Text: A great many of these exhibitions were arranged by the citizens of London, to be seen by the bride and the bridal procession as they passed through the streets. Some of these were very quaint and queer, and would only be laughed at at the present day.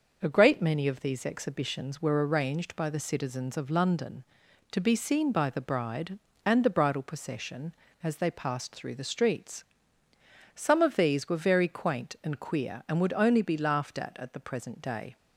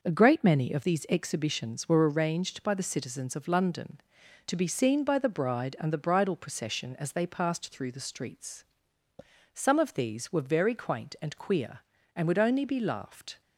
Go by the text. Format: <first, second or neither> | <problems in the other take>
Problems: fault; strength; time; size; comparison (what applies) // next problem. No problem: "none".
first | stops before "at at the present day"; at 13.4 s